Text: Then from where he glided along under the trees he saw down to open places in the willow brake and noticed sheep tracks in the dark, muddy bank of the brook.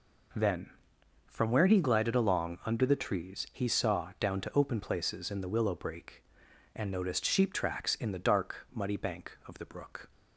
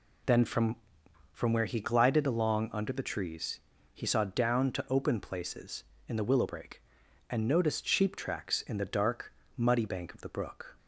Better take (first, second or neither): first